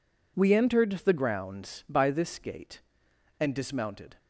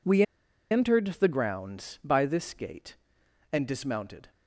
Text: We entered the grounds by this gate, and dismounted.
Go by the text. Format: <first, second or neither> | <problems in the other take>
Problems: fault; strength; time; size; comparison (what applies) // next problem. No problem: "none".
first | pauses between "We" and "entered"; noticeable; at 0.2 s; 0.48 s long